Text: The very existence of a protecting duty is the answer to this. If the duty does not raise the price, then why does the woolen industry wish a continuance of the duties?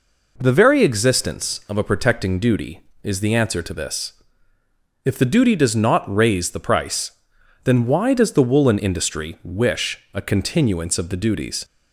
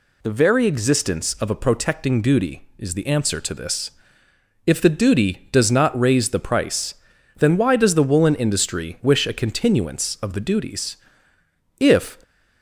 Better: first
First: none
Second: goes on to say "If"; slight; from 11.7 s on; 0.44 s long

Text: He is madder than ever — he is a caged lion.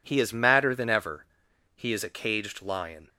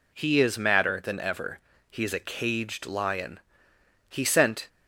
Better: first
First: none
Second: goes on to say "He sent"; from 4.0 s on; 0.60 s long

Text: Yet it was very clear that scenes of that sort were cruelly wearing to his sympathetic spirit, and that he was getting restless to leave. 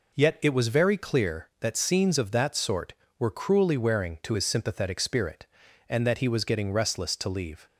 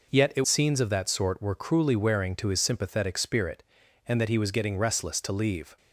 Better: first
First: none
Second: skips "was very clear that"; at 0.4 s

